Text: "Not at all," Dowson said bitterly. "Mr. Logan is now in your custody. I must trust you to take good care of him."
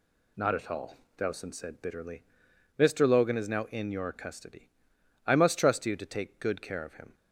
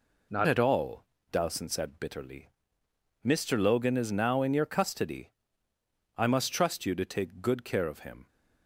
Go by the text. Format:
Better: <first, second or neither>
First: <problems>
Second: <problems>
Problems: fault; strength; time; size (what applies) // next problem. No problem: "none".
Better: first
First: none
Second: changes voice at "at"; from 0.4 s on; 7.8 s long